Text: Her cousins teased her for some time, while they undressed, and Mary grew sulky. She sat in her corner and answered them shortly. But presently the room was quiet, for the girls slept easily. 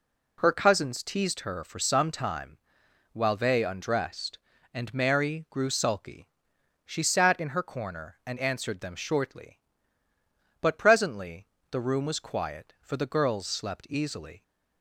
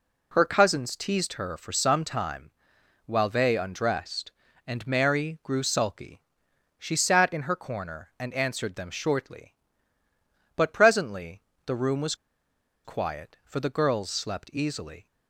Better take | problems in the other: first | pauses between "presently" and "the"; slight; at 11.4 s; 0.24 s long; slight in the first // pauses between "was" and "quiet"; noticeable; at 12.1 s; 0.70 s long

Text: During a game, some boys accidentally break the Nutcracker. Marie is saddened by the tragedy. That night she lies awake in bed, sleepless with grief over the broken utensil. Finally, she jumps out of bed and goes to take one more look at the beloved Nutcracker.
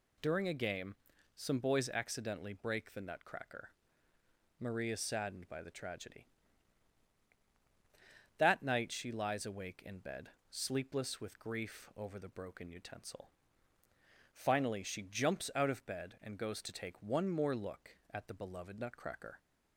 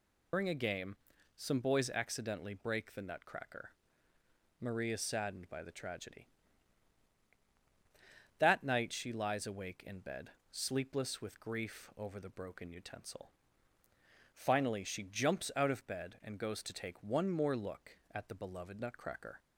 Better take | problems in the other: first | loses the start of "During"; at 0.3 s; 125 ms

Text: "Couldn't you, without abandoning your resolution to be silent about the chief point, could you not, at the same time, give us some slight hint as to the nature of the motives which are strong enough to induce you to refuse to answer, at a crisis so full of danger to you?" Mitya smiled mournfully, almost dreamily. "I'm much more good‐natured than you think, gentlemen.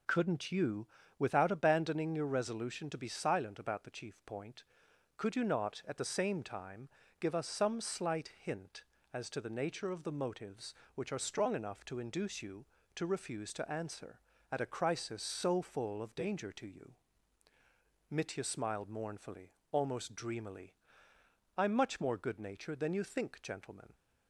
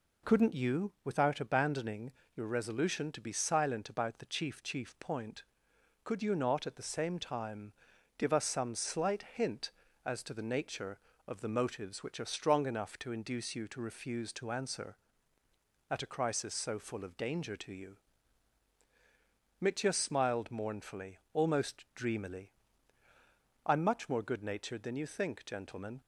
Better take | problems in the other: first | pauses between "abandoning" and "your"; slight; at 2.1 s; 0.24 s long // says "chief" twice; at 4.6 s

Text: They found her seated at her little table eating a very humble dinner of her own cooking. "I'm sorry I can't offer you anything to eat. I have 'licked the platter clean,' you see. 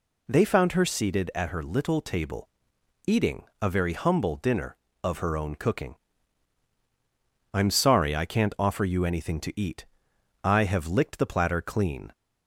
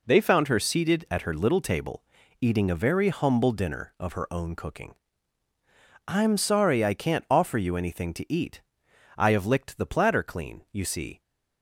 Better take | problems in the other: second | pauses between "table" and "eating"; noticeable; at 2.4 s; 0.56 s long; also in the second // pauses between "eating" and "a"; slight; at 3.4 s; 0.18 s long // stops before "you see"; at 12.1 s

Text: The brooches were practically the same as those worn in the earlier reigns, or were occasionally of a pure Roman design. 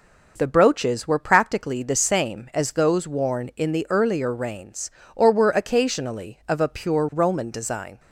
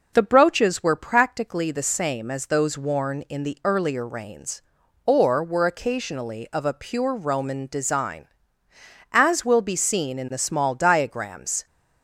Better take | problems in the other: first | goes on to say "As will be seen in the small diagrams"; strong; from 9.1 s on; 2.5 s long

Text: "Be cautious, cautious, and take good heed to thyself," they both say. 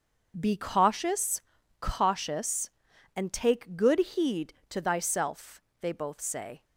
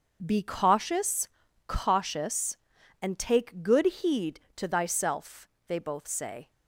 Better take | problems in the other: neither | starts louder than the rest; the same in both

